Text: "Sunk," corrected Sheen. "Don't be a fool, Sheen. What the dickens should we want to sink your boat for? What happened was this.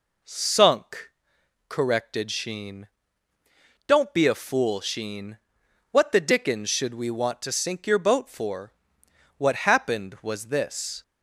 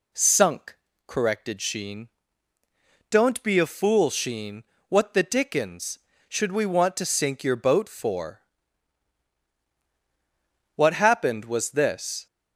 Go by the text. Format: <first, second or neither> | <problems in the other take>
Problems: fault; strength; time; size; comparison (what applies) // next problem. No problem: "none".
neither | none